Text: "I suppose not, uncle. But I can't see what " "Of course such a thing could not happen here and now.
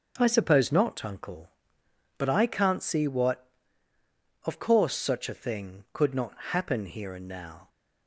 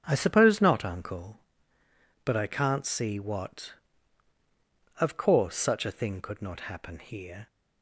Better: first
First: none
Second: starts louder than the rest; strong; until 1.0 s; 7.5 dB // stops before "and now"; at 7.4 s

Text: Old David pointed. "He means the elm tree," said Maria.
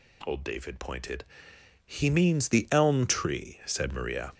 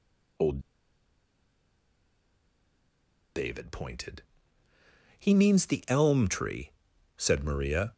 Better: first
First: none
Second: pauses between "Old" and "David"; strong; at 0.5 s; 2.7 s long

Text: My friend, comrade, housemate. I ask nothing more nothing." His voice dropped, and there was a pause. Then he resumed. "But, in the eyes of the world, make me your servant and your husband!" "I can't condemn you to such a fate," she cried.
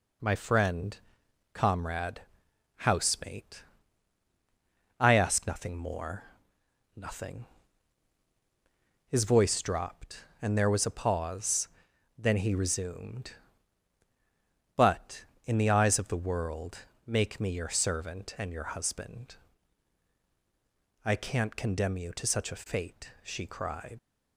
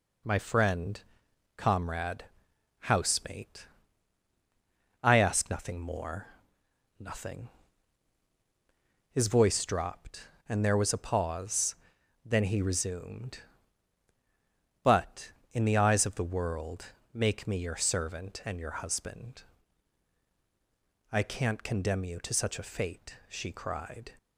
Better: second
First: pauses between "more" and "nothing"; noticeable; at 6.2 s; 0.70 s long // leaves "cried" unfinished; at 23.9 s; 125 ms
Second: pauses between "more" and "nothing"; noticeable; at 6.2 s; 0.70 s long

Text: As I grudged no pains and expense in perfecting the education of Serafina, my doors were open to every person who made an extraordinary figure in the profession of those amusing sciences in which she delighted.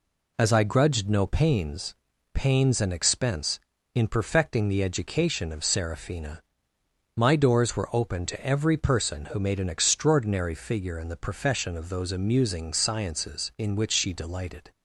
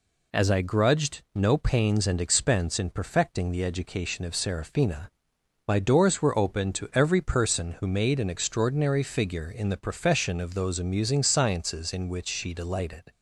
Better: second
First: says "pains" twice; at 2.3 s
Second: none

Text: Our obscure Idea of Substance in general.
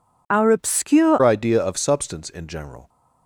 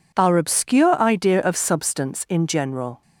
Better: second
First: changes voice at "Idea"; from 1.2 s on; 1.6 s long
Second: none

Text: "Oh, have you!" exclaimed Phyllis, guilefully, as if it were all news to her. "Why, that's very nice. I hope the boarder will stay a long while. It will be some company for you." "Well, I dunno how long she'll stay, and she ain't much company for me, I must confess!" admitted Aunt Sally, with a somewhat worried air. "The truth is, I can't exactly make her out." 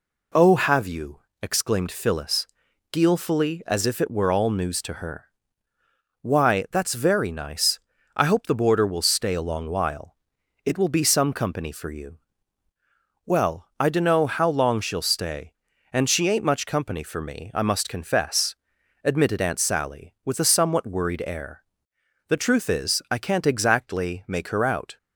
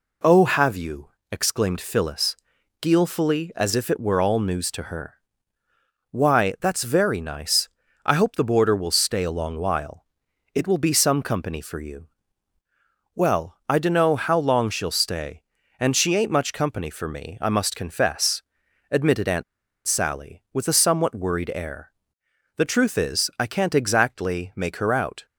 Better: first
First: none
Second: pauses between "Aunt" and "Sally"; at 19.4 s; 0.43 s long

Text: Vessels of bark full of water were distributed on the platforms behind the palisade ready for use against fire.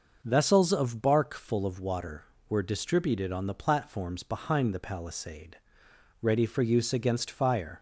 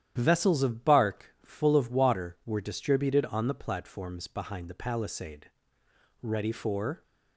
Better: first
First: starts louder than the rest; noticeable; until 1.2 s; 6 dB // pauses between "palisade" and "ready"; noticeable; at 5.5 s; 0.66 s long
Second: starts louder than the rest; strong; until 1.1 s; 10.5 dB // pauses between "palisade" and "ready"; noticeable; at 5.5 s; 0.72 s long // stops before "use against fire"; at 7.0 s

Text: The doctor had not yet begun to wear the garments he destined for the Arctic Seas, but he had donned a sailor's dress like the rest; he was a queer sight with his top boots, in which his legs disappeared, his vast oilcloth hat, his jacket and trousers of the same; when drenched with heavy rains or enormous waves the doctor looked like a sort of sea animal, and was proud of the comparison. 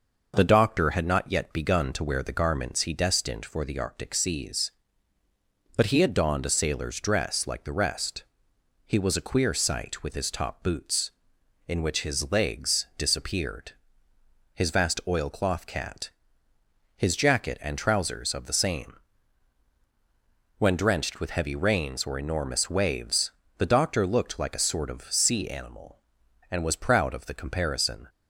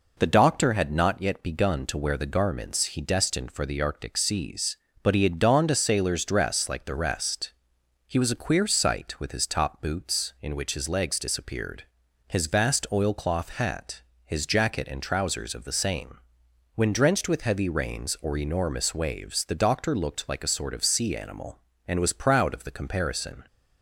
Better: second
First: says "cat" for "hat"; at 15.6 s // pauses between "waves" and "the"; slight; at 23.3 s; 0.28 s long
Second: none

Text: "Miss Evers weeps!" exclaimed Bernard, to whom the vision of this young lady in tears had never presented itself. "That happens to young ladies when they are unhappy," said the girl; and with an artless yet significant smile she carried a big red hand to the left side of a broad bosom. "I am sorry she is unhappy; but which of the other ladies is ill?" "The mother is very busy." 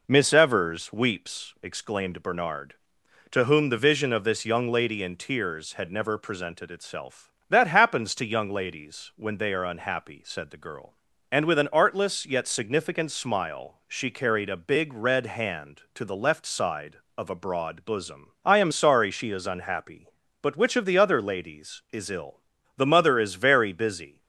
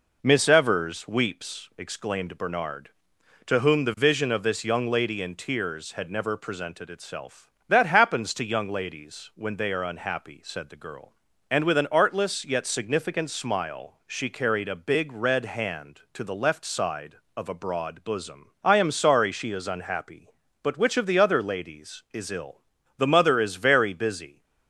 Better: neither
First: none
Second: none

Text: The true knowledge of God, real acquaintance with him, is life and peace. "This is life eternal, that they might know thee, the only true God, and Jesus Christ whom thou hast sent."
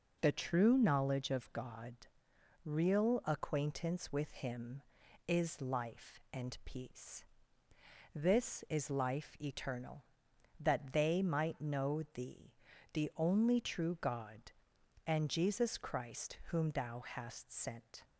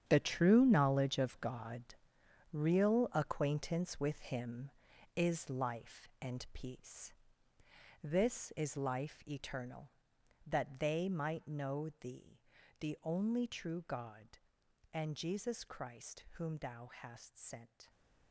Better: first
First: none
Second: gets quieter; strong; throughout; 12.5 dB

